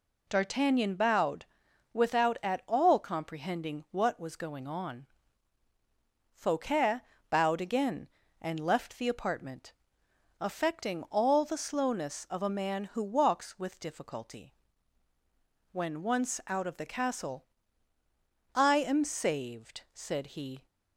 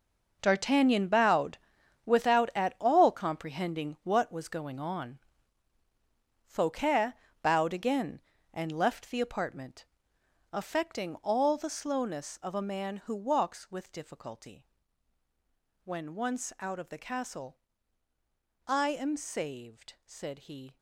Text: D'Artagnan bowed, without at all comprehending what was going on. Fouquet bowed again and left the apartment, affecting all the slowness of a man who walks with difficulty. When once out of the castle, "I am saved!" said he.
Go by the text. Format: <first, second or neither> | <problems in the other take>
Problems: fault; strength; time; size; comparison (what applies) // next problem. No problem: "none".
first | gets quieter; strong; throughout; 13.5 dB // pauses between "Fouquet" and "bowed"; slight; at 7.1 s; 0.28 s long; slight in the first